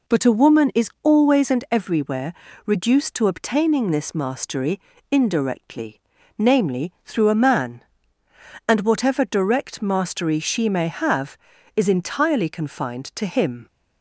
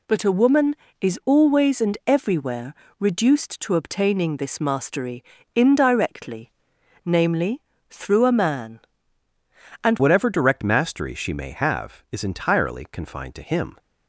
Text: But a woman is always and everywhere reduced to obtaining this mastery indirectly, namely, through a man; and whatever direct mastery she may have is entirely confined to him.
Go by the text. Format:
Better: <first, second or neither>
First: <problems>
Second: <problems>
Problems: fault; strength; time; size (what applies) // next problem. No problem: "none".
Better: first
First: pauses between "everywhere" and "reduced"; slight; at 2.3 s; 0.32 s long // pauses between "mastery" and "indirectly"; slight; at 4.7 s; 0.32 s long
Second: pauses between "everywhere" and "reduced"; slight; at 2.7 s; 0.26 s long // pauses between "mastery" and "indirectly"; slight; at 5.2 s; 0.32 s long // changes voice at "whatever"; from 9.9 s on; 3.8 s long